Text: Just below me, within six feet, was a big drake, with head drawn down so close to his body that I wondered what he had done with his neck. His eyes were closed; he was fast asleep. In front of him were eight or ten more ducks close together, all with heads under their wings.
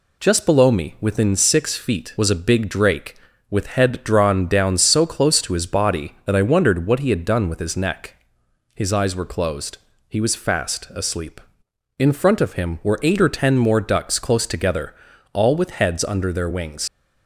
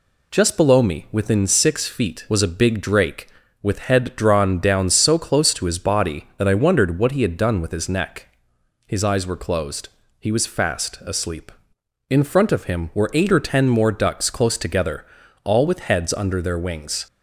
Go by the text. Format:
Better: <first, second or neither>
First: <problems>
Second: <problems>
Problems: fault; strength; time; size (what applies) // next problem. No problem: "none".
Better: second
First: leaves "wings" unfinished; at 16.8 s; 85 ms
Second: none